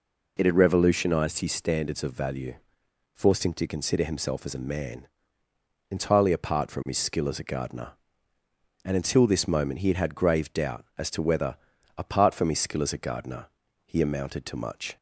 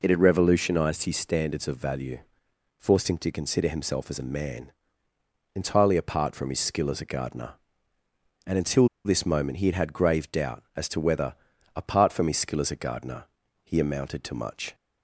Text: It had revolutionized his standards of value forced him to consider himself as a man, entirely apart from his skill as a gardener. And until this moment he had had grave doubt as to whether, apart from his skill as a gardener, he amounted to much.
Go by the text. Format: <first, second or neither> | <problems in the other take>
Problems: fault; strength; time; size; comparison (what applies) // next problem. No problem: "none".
first | pauses between "value" and "forced"; noticeable; at 2.1 s; 0.62 s long; noticeable in the first // pauses between "until" and "this"; slight; at 8.8 s; 0.16 s long